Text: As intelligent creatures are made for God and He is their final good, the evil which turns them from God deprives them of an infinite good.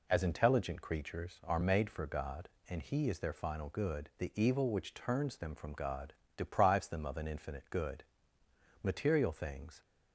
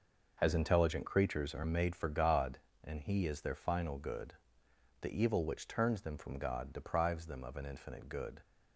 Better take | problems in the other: second | pauses between "God" and "deprives"; slight; at 6.1 s; 0.24 s long // goes on to say "Material things"; noticeable; from 8.8 s on; 0.98 s long

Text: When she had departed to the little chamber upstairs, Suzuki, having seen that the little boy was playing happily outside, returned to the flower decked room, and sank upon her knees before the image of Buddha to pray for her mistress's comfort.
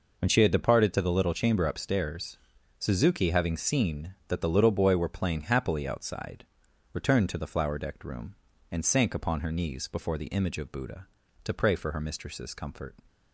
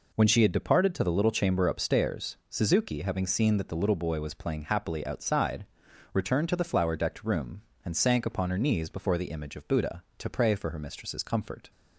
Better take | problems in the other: second | says "were" for "was"; at 4.9 s

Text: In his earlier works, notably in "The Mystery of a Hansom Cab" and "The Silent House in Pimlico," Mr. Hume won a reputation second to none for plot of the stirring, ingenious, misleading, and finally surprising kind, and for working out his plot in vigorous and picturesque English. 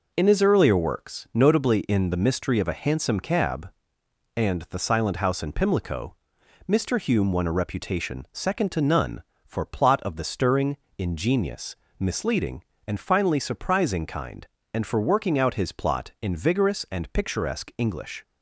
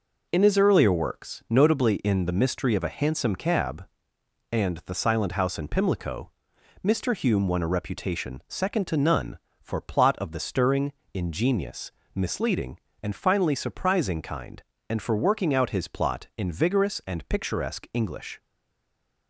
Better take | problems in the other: first | stays silent after the last word; slight; from 18.3 s on; 0.9 s long

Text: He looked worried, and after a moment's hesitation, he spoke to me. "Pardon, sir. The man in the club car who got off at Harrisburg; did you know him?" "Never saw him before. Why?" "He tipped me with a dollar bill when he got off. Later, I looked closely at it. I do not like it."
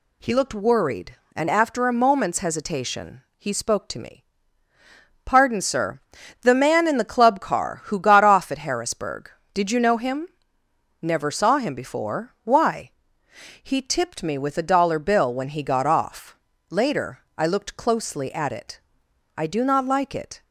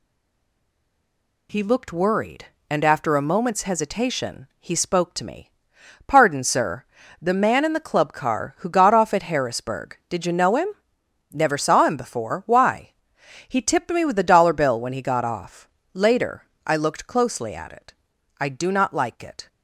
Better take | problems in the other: first | stays silent before the first word; noticeable; until 1.4 s; 1.4 s long

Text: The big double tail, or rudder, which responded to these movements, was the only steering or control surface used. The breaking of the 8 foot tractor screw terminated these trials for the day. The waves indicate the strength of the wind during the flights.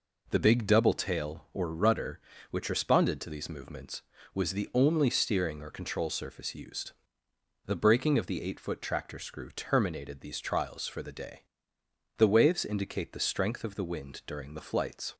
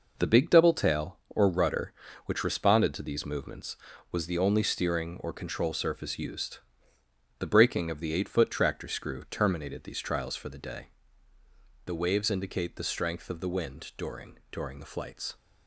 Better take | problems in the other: first | says "during" twice; at 14.5 s

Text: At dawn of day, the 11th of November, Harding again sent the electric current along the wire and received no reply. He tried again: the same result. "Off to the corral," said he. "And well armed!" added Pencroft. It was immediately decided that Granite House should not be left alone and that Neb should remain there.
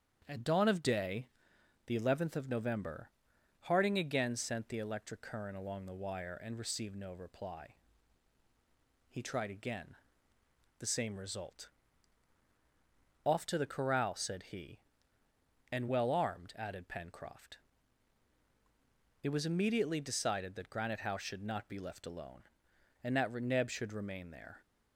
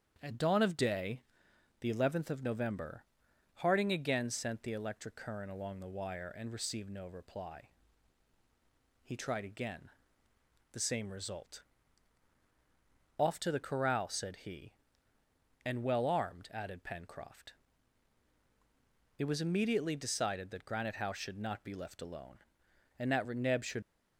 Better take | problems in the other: first | starts louder than the rest; strong; until 1.2 s; 8 dB; strong in the first // stops before "remain there"; at 23.8 s

